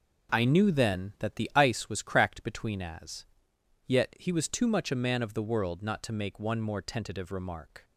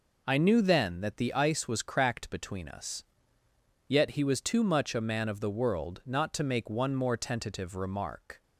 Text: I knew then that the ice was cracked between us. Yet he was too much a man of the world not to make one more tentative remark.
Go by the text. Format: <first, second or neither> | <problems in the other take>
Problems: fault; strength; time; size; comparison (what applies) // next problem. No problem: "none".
second | says "as" for "us"; at 2.8 s